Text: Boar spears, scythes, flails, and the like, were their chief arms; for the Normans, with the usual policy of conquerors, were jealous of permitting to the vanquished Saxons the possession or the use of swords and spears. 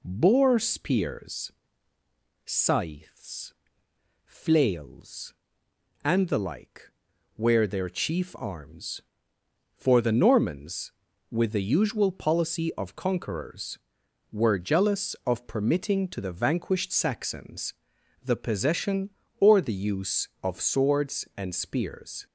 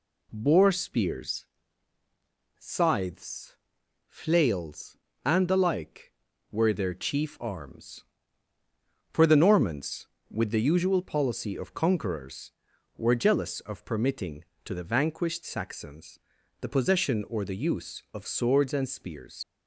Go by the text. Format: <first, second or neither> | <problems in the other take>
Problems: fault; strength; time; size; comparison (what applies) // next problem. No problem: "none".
first | pauses between "Saxons" and "the"; at 16.1 s; 0.42 s long; noticeable in the first // leaves "spears" unfinished; at 19.4 s; 65 ms